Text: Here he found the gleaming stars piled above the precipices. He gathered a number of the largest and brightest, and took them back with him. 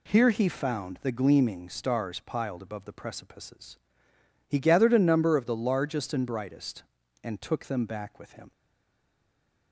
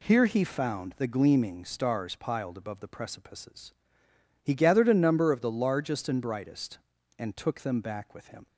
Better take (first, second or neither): second